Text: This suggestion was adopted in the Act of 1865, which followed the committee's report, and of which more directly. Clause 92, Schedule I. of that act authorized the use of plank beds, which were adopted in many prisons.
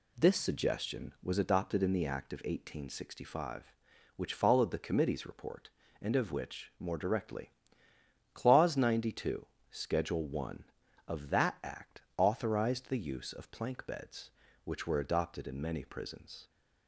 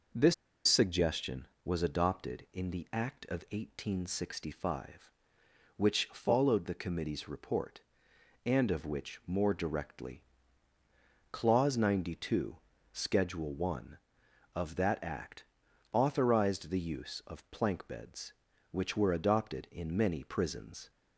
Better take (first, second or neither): first